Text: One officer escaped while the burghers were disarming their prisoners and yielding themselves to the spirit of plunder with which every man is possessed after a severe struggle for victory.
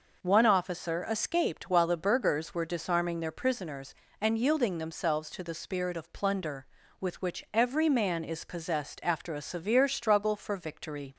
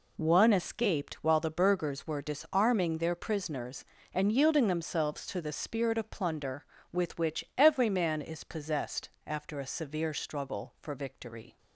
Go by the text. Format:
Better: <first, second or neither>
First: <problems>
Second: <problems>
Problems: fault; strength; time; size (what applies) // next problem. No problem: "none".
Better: first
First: none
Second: skips "officer"; at 0.5 s // pauses between "possessed" and "after"; slight; at 9.0 s; 0.16 s long